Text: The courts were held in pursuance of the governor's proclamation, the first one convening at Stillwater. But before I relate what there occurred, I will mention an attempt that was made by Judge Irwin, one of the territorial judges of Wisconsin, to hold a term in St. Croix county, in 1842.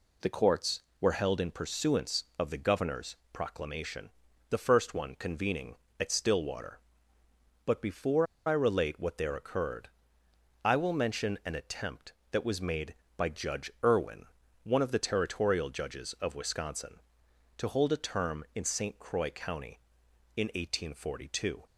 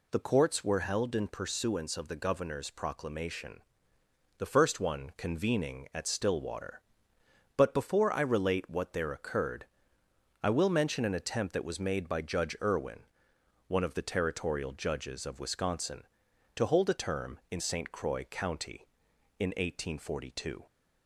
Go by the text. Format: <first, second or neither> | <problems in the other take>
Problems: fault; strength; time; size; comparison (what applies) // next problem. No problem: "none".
second | pauses between "governor's" and "proclamation"; slight; at 3.1 s; 0.18 s long // pauses between "before" and "I"; slight; at 8.2 s; 0.21 s long